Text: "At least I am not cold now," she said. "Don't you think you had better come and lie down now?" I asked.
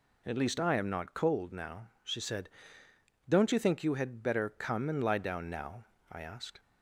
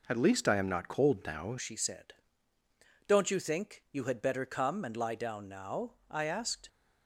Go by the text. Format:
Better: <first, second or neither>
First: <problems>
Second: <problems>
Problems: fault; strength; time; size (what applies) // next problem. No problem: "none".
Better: first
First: none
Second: changes voice at "she"; from 1.5 s on; 5.1 s long